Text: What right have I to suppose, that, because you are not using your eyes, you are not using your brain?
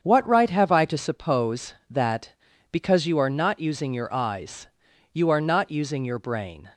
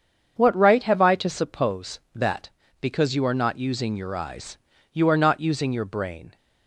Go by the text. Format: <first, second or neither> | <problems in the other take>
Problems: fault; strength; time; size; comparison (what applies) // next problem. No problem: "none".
neither | starts louder than the rest; strong; the same in both